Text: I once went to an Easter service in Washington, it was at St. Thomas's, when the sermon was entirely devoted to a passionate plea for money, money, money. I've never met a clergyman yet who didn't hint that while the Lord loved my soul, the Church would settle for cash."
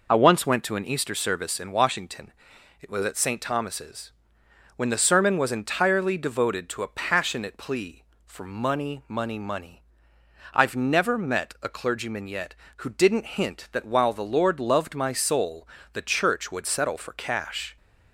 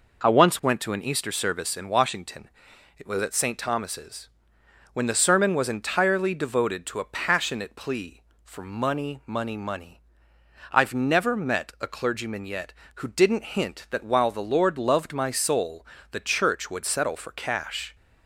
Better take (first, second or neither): second